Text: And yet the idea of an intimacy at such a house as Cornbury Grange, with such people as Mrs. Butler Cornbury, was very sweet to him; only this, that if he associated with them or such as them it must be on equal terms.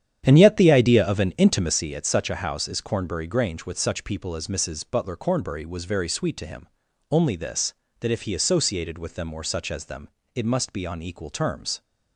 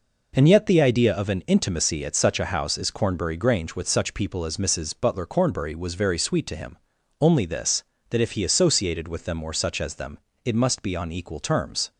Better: second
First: starts louder than the rest; strong; until 1.8 s; 9.5 dB // pauses between "them" and "it"; slight; at 10.0 s; 0.26 s long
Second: pauses between "them" and "it"; slight; at 10.1 s; 0.26 s long

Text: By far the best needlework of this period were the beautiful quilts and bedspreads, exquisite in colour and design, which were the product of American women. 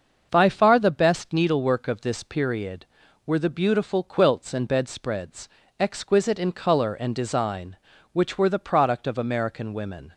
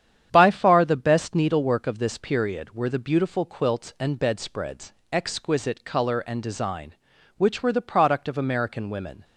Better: first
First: starts louder than the rest; until 1.3 s; 6.5 dB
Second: starts louder than the rest; strong; until 1.3 s; 9 dB // skips "in"; at 5.8 s

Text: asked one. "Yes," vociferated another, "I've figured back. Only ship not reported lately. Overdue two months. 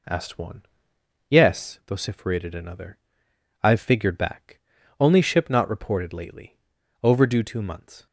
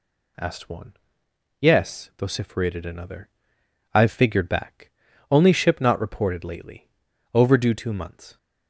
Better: second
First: starts louder than the rest; until 1.8 s; 3.5 dB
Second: none

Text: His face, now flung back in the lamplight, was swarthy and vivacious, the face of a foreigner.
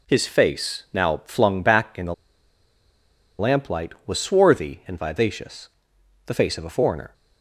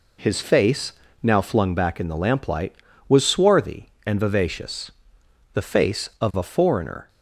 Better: second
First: pauses between "the" and "lamplight"; strong; at 2.1 s; 1.2 s long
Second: none

